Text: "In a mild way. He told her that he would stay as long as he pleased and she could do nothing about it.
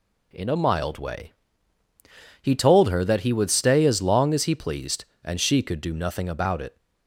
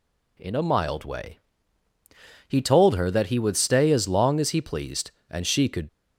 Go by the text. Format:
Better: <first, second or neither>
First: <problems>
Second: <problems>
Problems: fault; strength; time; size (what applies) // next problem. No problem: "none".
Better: first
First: none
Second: stops before "do nothing about it"; at 5.8 s